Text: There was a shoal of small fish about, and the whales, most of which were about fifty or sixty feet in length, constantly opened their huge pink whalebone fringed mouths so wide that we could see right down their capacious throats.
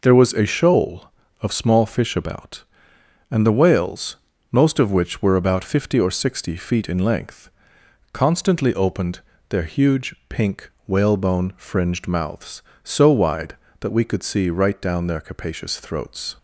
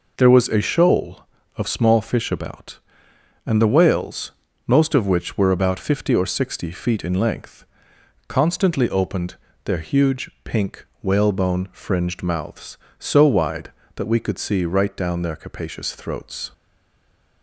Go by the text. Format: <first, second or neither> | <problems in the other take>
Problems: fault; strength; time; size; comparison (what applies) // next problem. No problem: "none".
first | pauses between "opened" and "their"; slight; at 9.3 s; 0.30 s long; slight in the first // pauses between "huge" and "pink"; slight; at 10.2 s; 0.16 s long; slight in the first // pauses between "pink" and "whalebone"; slight; at 10.8 s; 0.16 s long; slight in the first // stays silent after the last word; slight; from 16.5 s on; 0.9 s long